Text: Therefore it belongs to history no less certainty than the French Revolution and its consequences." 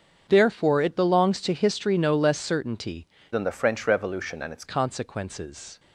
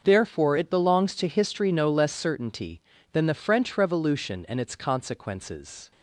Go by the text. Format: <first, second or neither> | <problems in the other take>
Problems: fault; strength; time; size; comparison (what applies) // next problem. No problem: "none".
second | starts louder than the rest; until 1.3 s; 7 dB; also in the second // changes voice from "than" to "its"; from 3.3 to 4.6 s; 1.3 s long